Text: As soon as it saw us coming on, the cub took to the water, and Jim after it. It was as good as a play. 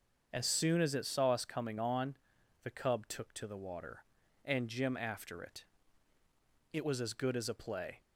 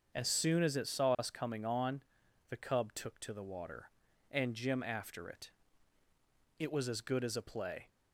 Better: neither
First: starts louder than the rest; until 1.3 s; 6.5 dB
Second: starts louder than the rest; until 1.2 s; 6.5 dB

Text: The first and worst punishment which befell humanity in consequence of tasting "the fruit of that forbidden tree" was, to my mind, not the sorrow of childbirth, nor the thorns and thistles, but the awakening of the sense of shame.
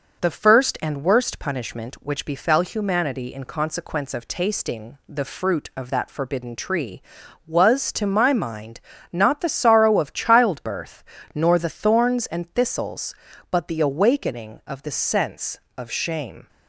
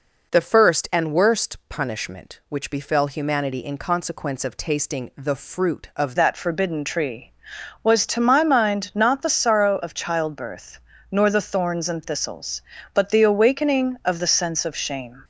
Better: first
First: none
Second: changes voice at "that"; from 6.1 s on; 9.1 s long

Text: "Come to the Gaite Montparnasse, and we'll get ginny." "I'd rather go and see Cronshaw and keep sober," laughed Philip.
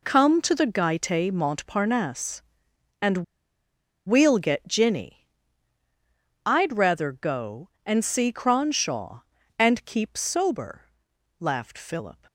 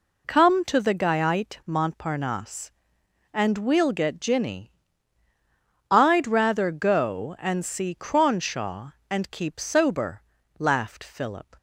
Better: second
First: pauses between "and" and "we'll"; noticeable; at 3.1 s; 0.89 s long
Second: none

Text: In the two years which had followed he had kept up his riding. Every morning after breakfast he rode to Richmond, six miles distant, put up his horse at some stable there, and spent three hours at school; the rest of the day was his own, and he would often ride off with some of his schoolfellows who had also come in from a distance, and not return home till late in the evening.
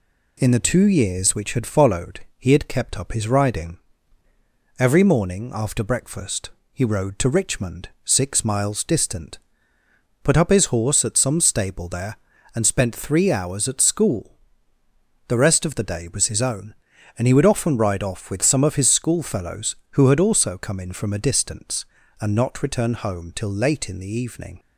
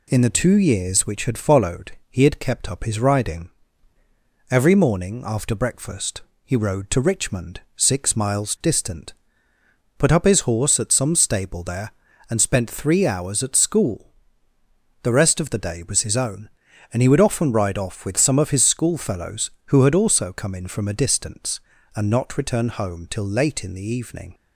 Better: neither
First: pauses between "followed" and "he"; slight; at 2.1 s; 0.18 s long // pauses between "breakfast" and "he"; slight; at 6.5 s; 0.20 s long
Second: pauses between "followed" and "he"; slight; at 1.9 s; 0.18 s long // pauses between "breakfast" and "he"; slight; at 6.2 s; 0.20 s long

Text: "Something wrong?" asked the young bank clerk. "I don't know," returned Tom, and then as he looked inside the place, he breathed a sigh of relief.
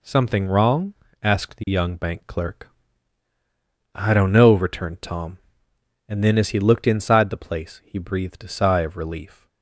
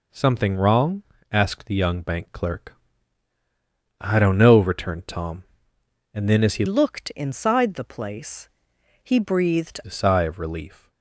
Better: first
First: none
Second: changes voice from "looked" to "breathed"; from 6.6 to 9.7 s; 3.1 s long

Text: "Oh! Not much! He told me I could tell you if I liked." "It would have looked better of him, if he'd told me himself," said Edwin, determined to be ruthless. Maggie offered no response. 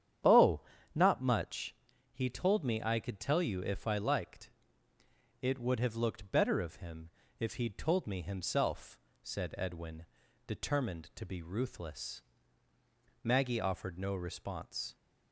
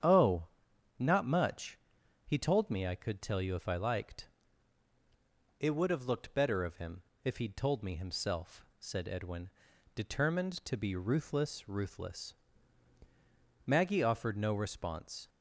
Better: first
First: starts louder than the rest; strong; until 1.5 s; 9.5 dB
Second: starts louder than the rest; strong; until 1.5 s; 9 dB // says "ruthless" twice; at 11.6 s

